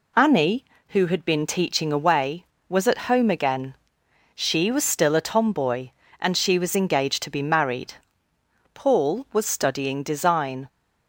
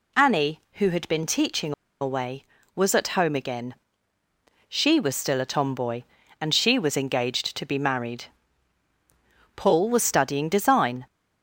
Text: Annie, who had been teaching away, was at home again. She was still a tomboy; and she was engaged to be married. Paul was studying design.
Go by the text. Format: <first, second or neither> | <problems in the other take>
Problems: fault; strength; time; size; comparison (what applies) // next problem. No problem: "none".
first | pauses between "teaching" and "away"; slight; at 1.7 s; 0.29 s long